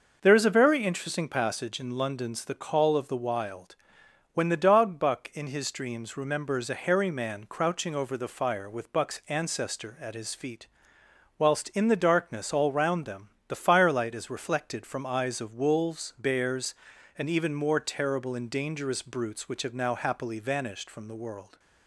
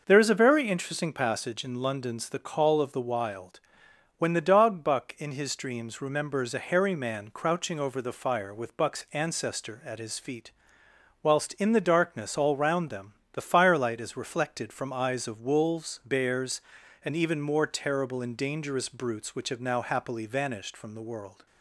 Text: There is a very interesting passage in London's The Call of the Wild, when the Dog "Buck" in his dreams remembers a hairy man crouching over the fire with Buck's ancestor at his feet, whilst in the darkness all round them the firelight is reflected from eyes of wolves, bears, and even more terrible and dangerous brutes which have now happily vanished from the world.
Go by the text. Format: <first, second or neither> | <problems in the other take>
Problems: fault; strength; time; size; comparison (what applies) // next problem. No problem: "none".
neither | pauses between "them" and "the"; slight; the same in both